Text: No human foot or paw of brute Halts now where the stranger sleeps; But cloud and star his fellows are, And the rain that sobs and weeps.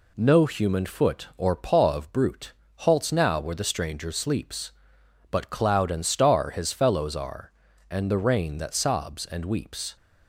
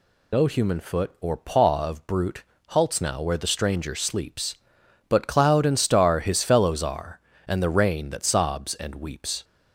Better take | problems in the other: first | loses the start of "No"; at 0.3 s; 70 ms // pauses between "brute" and "Halts"; slight; at 2.4 s; 0.24 s long; slight in the first

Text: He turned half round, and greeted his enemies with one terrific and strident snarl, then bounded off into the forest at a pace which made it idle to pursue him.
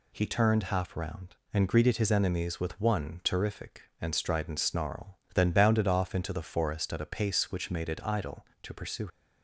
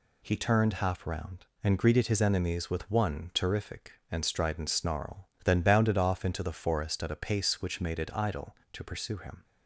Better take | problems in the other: second | stops before "him"; at 9.0 s

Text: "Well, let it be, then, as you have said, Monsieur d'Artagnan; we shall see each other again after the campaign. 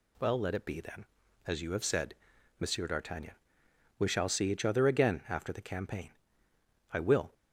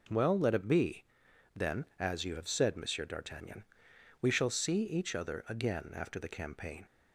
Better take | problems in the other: second | goes on to say "I will"; slight; from 6.9 s on; 0.42 s long

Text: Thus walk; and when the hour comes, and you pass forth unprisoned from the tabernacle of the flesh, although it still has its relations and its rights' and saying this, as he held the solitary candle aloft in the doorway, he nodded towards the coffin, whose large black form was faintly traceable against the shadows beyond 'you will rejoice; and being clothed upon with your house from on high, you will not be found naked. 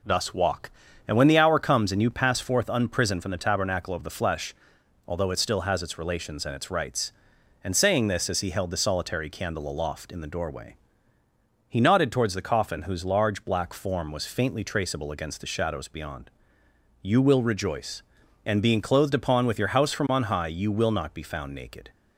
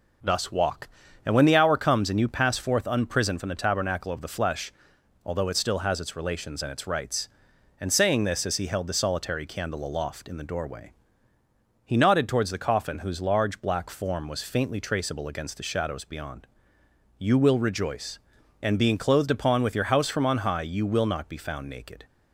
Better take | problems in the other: neither | pauses between "beyond" and "you"; noticeable; the same in both

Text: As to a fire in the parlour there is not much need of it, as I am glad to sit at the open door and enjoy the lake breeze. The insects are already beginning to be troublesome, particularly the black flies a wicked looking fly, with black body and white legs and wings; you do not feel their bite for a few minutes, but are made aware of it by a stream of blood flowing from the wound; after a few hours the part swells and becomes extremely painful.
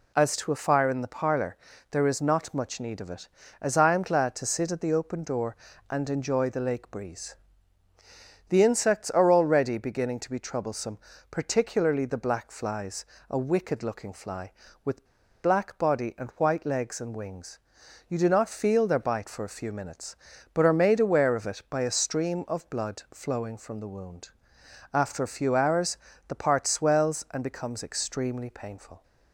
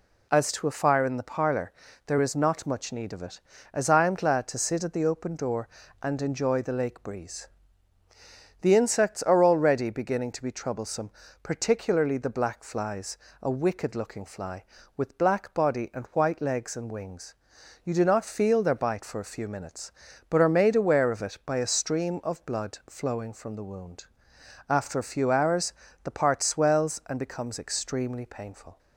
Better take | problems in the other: second | pauses between "parlour" and "there"; slight; at 1.5 s; 0.36 s long; slight in the second // pauses between "flies" and "a"; slight; at 13.0 s; 0.24 s long; slight in the second // pauses between "with" and "black"; at 15.0 s; 0.37 s long // pauses between "hours" and "the"; slight; at 25.9 s; 0.32 s long; slight in the second

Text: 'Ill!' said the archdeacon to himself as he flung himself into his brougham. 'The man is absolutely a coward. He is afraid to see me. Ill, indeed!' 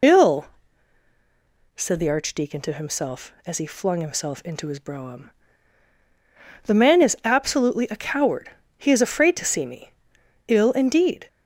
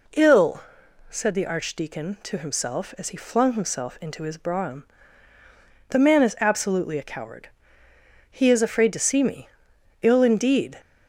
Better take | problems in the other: second | loses the start of "Ill"; at 0.0 s; 30 ms

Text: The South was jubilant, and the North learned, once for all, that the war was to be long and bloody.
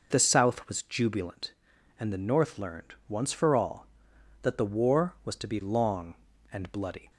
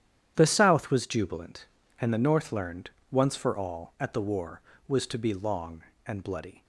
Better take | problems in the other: first | starts louder than the rest; strong; until 1.3 s; 10 dB // says "at" for "that"; at 3.9 s

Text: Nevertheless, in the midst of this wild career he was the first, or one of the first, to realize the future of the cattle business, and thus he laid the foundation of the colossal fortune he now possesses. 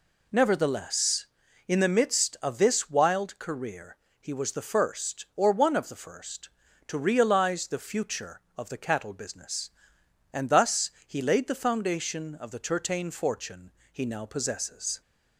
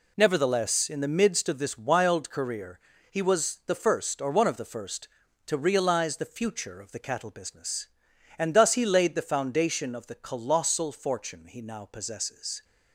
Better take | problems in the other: second | pauses between "career" and "he"; slight; at 3.9 s; 0.22 s long; slight in the second // pauses between "thus" and "he"; slight; at 10.9 s; 0.16 s long // says "tertain" for "colossal"; at 12.5 s // pauses between "fortune" and "he"; slight; at 13.7 s; 0.20 s long

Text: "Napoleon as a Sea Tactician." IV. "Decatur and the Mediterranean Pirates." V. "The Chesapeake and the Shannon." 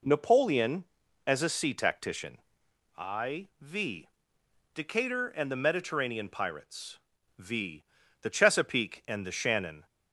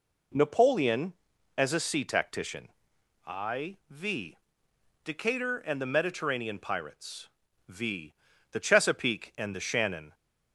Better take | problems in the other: neither | none

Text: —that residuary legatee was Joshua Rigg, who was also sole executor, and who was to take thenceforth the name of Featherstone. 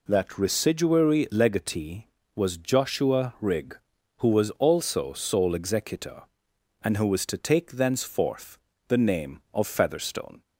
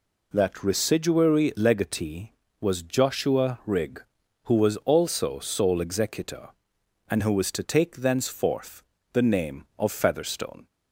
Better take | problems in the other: neither | pauses between "thenceforth" and "the"; slight; the same in both

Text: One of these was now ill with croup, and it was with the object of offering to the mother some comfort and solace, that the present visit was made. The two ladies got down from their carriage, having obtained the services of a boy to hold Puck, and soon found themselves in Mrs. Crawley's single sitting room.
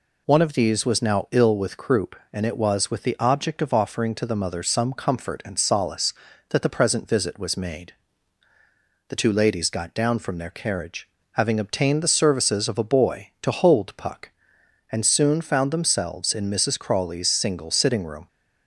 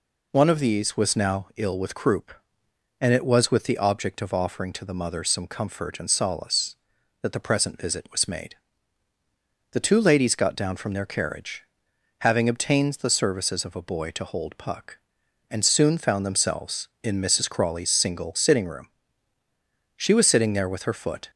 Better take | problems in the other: first | goes on to say "She was sitting there with her foot"; from 19.9 s on; 1.3 s long

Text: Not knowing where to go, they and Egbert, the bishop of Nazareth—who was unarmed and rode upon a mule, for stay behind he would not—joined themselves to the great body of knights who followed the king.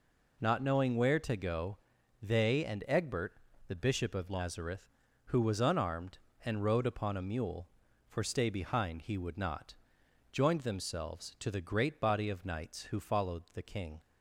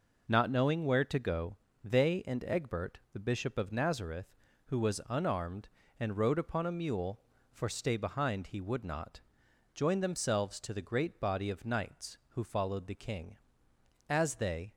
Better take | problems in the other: first | goes on to say "As they"; noticeable; from 14.0 s on; 0.66 s long

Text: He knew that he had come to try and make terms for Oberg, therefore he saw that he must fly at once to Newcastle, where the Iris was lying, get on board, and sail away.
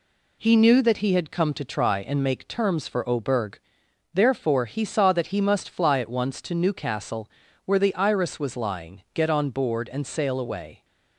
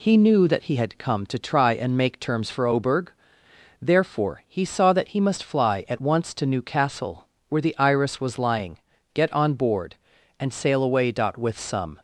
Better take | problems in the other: first | goes on to say "With some"; noticeable; from 11.3 s on; 0.64 s long

